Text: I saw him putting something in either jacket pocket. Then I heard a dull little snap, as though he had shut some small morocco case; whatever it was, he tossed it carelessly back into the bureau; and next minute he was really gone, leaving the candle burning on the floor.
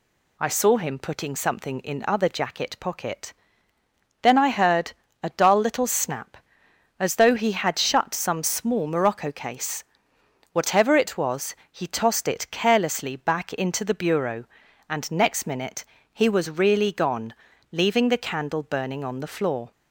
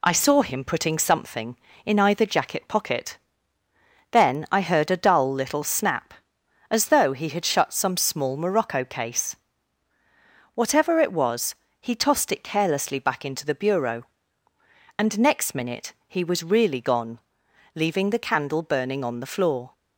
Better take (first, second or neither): second